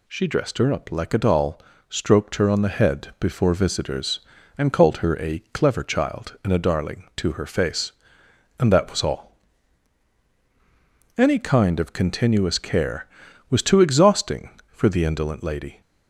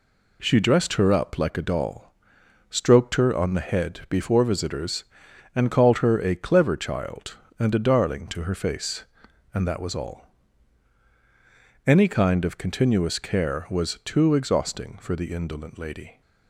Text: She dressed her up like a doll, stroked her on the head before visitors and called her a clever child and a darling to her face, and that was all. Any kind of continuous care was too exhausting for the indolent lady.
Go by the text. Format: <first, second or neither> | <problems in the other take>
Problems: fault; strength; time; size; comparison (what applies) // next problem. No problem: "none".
neither | none